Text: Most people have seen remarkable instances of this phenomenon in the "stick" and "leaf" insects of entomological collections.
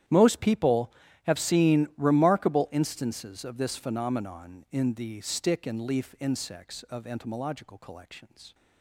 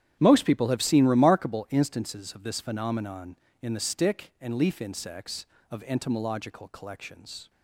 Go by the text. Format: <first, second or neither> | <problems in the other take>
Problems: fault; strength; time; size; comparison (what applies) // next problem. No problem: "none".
neither | starts louder than the rest; strong; the same in both